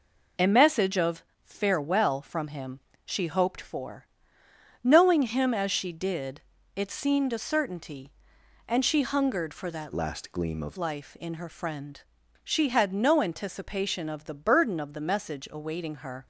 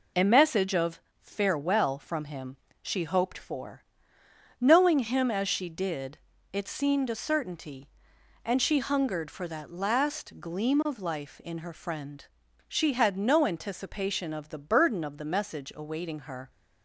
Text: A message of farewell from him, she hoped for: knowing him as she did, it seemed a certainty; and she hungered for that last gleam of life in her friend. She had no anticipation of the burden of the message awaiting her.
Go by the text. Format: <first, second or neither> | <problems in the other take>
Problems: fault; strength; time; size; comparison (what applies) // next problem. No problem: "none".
second | pauses between "of" and "farewell"; slight; at 1.2 s; 0.22 s long; slight in the second // changes voice from "last" to "of"; from 9.9 to 10.7 s; 0.8 s long